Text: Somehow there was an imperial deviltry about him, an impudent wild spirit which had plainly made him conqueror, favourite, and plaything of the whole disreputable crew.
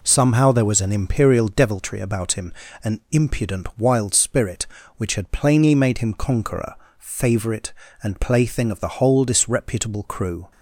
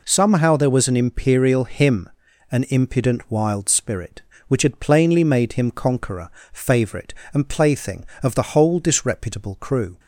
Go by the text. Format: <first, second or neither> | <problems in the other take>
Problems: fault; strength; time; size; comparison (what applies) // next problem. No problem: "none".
first | skips "deviltry about"; at 1.6 s